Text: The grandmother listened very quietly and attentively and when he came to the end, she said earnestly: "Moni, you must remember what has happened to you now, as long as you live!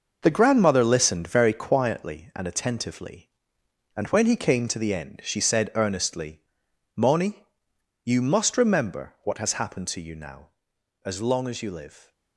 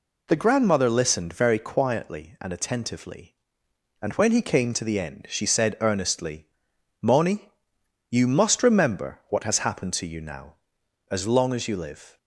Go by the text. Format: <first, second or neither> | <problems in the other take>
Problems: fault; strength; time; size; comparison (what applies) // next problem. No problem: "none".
second | gets quieter; strong; throughout; 9 dB